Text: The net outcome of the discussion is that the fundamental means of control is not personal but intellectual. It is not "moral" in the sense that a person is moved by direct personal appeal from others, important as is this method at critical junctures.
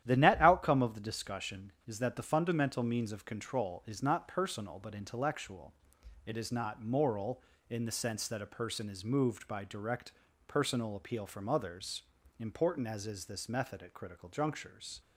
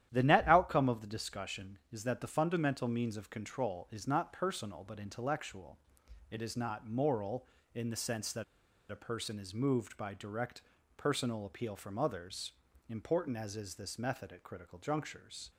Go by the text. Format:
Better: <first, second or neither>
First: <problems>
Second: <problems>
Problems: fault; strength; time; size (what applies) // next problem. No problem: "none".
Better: first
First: starts louder than the rest; strong; until 1.0 s; 11 dB // pauses between "direct" and "personal"; slight; at 10.1 s; 0.34 s long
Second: starts louder than the rest; strong; until 1.1 s; 11.5 dB // pauses between "that" and "a"; noticeable; at 8.4 s; 0.47 s long // pauses between "direct" and "personal"; slight; at 10.6 s; 0.34 s long